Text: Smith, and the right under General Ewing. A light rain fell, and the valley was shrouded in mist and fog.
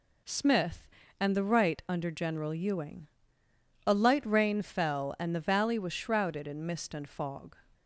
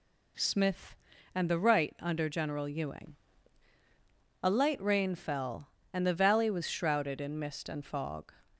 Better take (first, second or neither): neither